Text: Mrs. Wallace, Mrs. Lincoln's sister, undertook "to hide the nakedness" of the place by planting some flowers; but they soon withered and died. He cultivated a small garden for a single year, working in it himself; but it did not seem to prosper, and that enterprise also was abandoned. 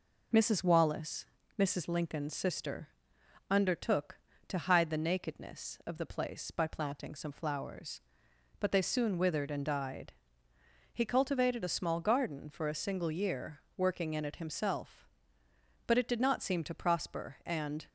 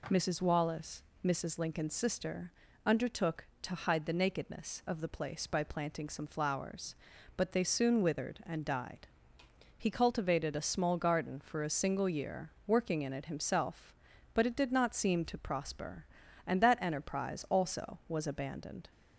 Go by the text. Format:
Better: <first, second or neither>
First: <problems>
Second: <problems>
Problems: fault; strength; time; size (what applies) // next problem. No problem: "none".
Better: second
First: stops before "that enterprise also was abandoned"; at 17.8 s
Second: none